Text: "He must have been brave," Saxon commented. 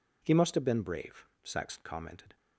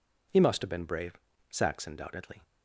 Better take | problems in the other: first | says "doubtedly" for "commented"; at 1.9 s

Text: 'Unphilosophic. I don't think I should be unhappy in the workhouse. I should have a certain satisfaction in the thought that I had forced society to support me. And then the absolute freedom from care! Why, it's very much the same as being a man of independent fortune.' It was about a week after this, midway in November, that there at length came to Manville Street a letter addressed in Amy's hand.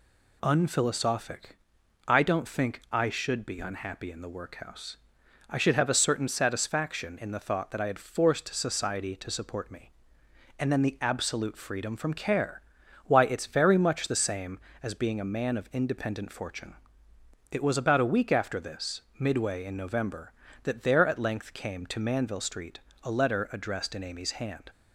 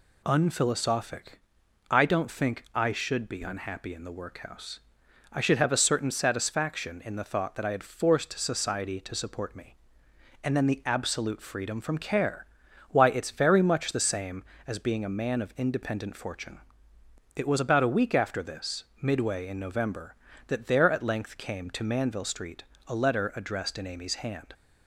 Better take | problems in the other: neither | pauses between "Street" and "a"; slight; the same in both

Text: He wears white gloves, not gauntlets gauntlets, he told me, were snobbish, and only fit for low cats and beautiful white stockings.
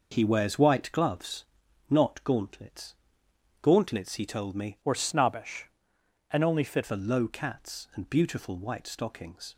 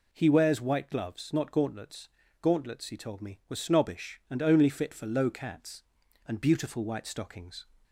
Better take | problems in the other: second | pauses between "gauntlets" and "gauntlets"; noticeable; at 2.9 s; 0.70 s long; slight in the second // changes voice from "were" to "fit"; from 4.8 to 6.8 s; 2.0 s long

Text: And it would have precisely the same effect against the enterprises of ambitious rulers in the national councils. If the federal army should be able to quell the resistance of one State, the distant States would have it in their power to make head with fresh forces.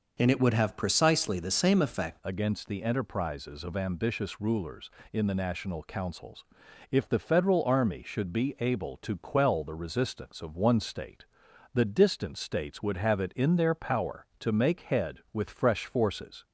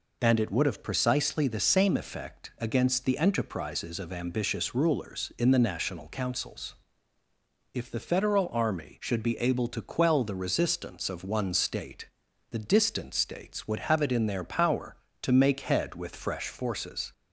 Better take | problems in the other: second | changes voice at "against"; from 2.2 s on; 14.2 s long

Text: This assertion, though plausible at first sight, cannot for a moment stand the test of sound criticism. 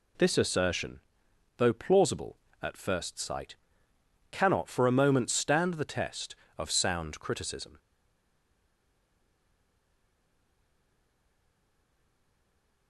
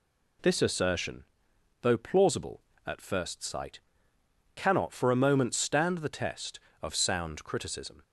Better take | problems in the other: second | stays silent after the last word; strong; from 7.7 s on; 5.1 s long

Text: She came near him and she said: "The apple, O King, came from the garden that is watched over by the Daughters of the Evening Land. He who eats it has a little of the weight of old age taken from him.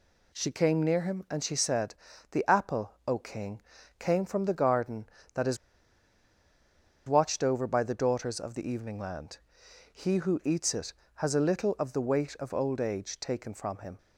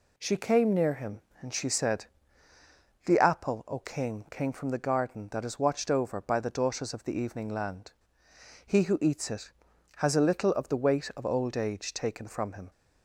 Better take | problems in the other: second | pauses between "is" and "watched"; strong; at 5.5 s; 1.5 s long

